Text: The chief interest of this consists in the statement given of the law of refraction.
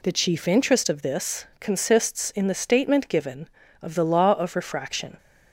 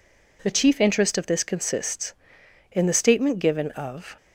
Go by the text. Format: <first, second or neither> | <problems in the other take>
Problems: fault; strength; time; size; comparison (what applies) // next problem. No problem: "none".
first | stops before "the law of refraction"; at 4.1 s